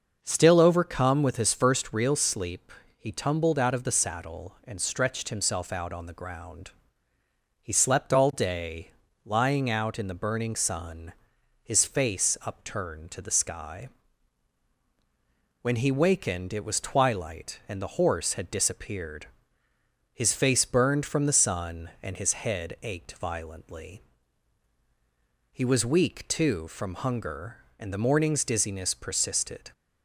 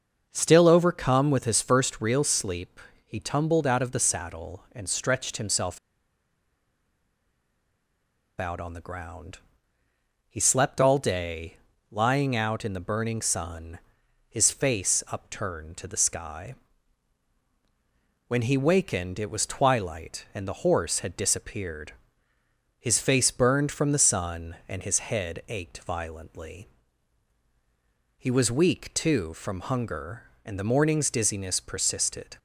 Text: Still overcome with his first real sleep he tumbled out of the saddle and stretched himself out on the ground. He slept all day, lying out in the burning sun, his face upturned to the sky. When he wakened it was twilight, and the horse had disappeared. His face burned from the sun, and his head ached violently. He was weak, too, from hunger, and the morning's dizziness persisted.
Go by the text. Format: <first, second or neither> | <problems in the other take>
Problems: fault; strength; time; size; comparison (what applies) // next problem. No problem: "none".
first | starts louder than the rest; noticeable; until 1.3 s; 6 dB; noticeable in the first // pauses between "sleep" and "he"; slight; at 2.7 s; 0.28 s long; slight in the first // pauses between "himself" and "out"; strong; at 5.7 s; 2.6 s long